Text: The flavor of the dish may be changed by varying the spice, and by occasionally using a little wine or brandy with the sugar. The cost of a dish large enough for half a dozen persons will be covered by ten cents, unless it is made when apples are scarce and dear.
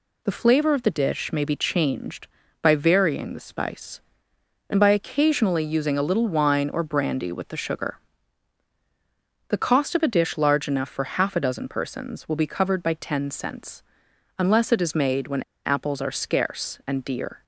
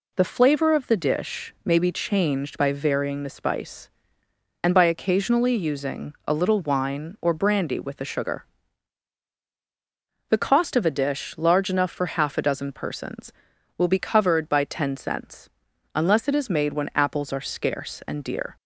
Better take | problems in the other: second | pauses between "when" and "apples"; slight; at 15.4 s; 0.23 s long

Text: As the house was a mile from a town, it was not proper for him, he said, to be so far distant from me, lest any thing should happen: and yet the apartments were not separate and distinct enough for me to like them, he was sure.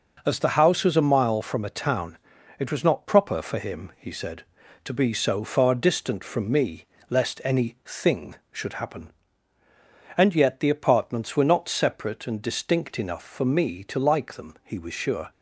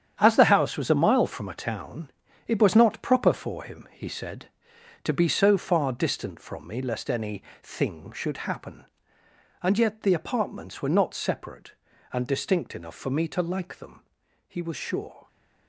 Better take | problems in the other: first | gets quieter; strong; throughout; 10 dB // pauses between "any" and "thing"; slight; at 7.4 s; 0.20 s long

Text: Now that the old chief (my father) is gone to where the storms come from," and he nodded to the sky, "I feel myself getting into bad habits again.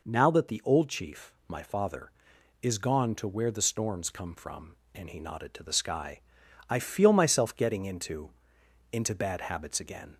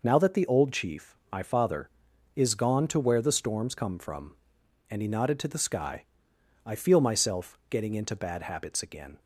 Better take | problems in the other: second | says "into" twice; at 8.9 s

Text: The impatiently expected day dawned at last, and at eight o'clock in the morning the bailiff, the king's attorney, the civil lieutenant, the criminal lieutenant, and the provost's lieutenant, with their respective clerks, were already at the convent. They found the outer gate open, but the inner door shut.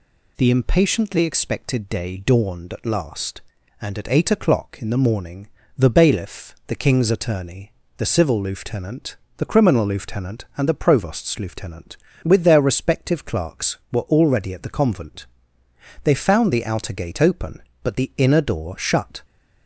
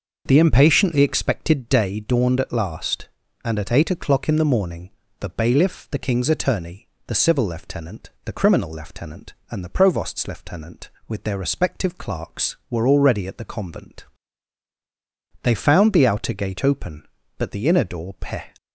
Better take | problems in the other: first | pauses between "morning" and "the"; slight; at 4.8 s; 0.30 s long; slight in the first // says "peh" for "shut"; at 18.1 s

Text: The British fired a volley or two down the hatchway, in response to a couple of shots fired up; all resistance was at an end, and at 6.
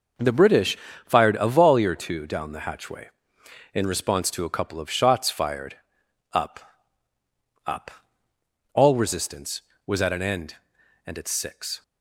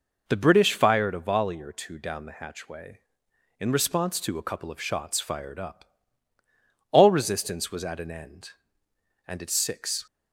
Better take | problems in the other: second | pauses between "British" and "fired"; slight; at 0.7 s; 0.28 s long // pauses between "fired" and "up"; noticeable; at 5.7 s; 0.58 s long // says "up" twice; at 7.6 s

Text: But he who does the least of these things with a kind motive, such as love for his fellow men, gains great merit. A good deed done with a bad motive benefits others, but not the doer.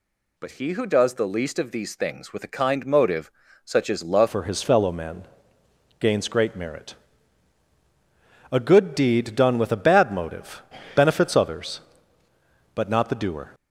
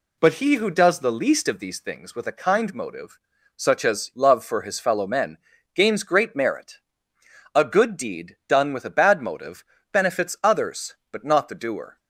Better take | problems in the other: second | changes voice at "for"; from 4.2 s on; 9.3 s long // pauses between "motive" and "benefits"; slight; at 10.6 s; 0.32 s long; slight in the second

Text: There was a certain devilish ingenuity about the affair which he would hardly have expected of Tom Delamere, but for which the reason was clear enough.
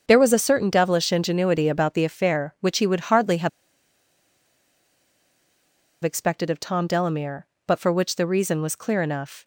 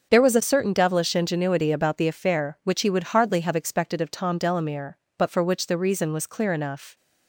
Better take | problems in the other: second | starts louder than the rest; until 1.0 s; 6 dB; also in the second // pauses between "have" and "expected"; strong; at 3.4 s; 2.5 s long

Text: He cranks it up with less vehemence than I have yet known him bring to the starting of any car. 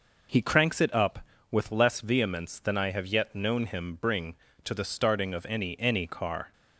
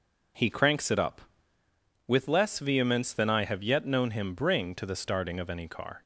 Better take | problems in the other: second | says "any" twice; at 5.8 s

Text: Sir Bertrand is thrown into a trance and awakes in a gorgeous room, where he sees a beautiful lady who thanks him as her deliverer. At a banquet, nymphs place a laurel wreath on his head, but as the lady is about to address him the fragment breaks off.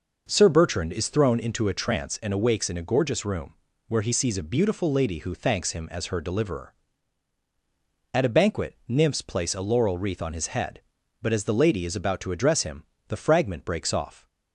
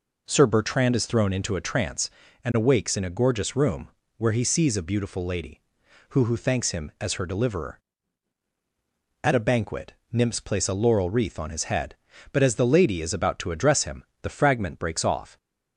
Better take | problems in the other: first | says "who" twice; at 6.2 s // pauses between "him" and "the"; slight; at 14.0 s; 0.20 s long; slight in the first

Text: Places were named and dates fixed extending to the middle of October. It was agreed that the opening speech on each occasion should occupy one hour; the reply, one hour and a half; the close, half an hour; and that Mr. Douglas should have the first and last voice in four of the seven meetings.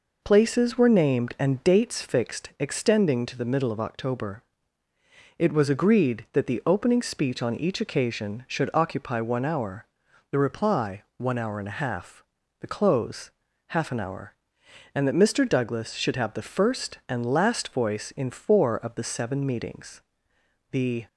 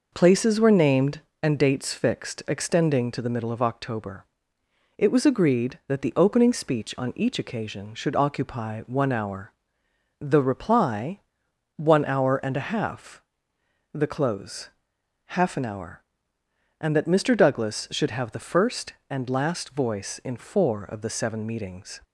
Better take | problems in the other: second | goes on to say "The"; slight; from 20.7 s on; 0.36 s long

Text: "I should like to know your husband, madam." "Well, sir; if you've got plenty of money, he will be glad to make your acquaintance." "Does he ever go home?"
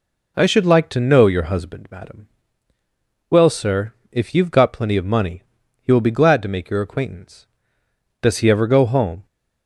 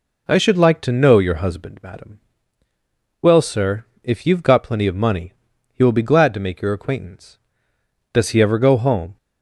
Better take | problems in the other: neither | none

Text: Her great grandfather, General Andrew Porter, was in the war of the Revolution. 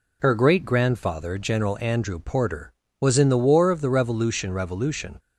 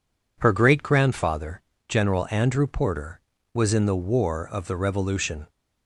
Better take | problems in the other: second | says "Revolution" twice; at 4.5 s

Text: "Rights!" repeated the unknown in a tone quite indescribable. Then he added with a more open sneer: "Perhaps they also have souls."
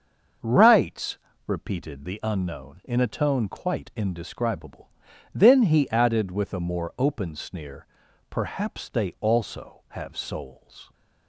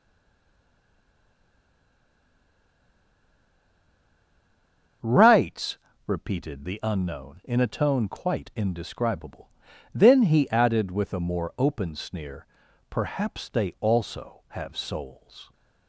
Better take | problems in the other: first | stays silent before the first word; strong; until 5.0 s; 5.0 s long // starts louder than the rest; until 6.3 s; 6.5 dB; also in the first

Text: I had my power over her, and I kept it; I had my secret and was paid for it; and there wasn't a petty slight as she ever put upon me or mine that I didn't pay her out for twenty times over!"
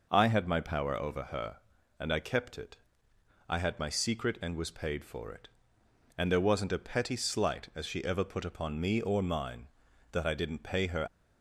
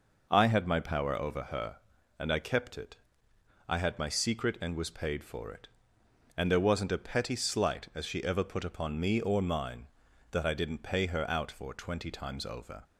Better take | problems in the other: second | stops before "out for twenty times over"; at 11.0 s

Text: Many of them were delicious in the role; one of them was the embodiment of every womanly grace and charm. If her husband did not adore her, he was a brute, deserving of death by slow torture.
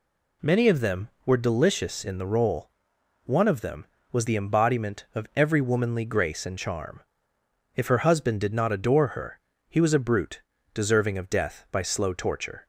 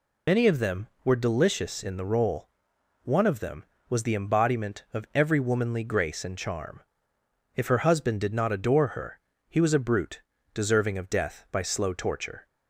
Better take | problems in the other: first | loses the start of "Many"; at 0.2 s; 70 ms

